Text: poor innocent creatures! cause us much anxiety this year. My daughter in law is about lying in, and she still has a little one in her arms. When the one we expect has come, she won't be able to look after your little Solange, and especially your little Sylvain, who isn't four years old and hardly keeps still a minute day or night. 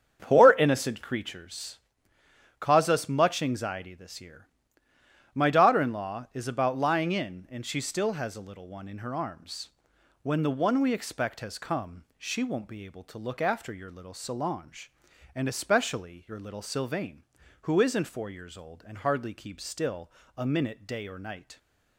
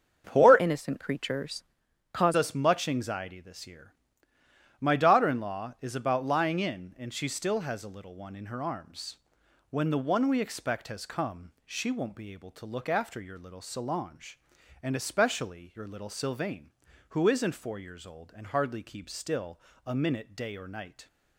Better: first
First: starts louder than the rest; strong; until 1.2 s; 7.5 dB // pauses between "still" and "a"; slight; at 20.0 s; 0.26 s long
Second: starts louder than the rest; until 1.2 s; 7 dB // changes voice from "innocent" to "cause"; from 0.5 to 2.3 s; 1.8 s long // pauses between "still" and "a"; slight; at 19.5 s; 0.26 s long

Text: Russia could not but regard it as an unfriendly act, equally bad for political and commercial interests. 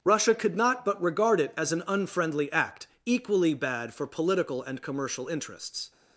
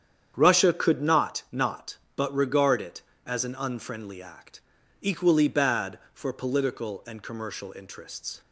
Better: first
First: starts louder than the rest; strong; until 1.0 s; 7.5 dB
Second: starts louder than the rest; strong; until 1.3 s; 8.5 dB // says "not" twice; at 1.5 s

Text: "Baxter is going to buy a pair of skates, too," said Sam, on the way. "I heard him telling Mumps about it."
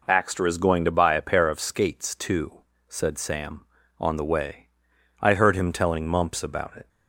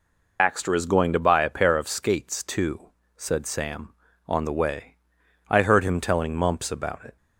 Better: first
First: none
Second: loses the start of "Baxter"; at 0.3 s; 75 ms

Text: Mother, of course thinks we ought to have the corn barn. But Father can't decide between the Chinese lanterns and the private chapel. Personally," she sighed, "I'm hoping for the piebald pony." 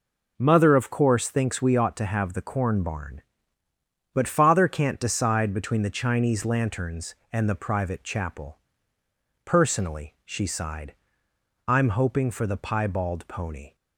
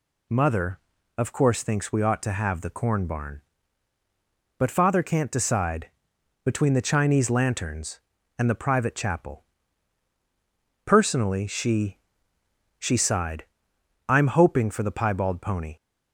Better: first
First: none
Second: pauses between "decide" and "between"; noticeable; at 5.8 s; 0.56 s long // says "she" twice; at 12.7 s

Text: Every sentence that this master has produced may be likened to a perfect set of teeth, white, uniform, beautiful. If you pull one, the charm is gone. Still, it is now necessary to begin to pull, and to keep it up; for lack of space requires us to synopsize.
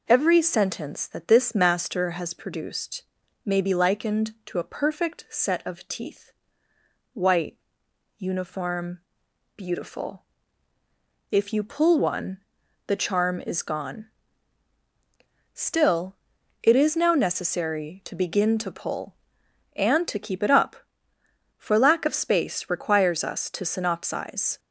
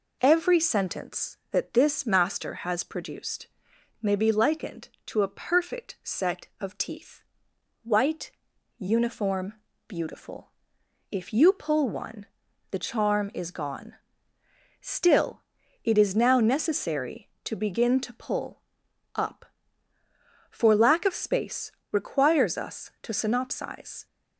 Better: first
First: pauses between "produced" and "may"; at 3.0 s; 0.42 s long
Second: pauses between "produced" and "may"; noticeable; at 3.4 s; 0.56 s long // skips "and to keep it"; at 18.8 s // pauses between "space" and "requires"; slight; at 21.6 s; 0.22 s long

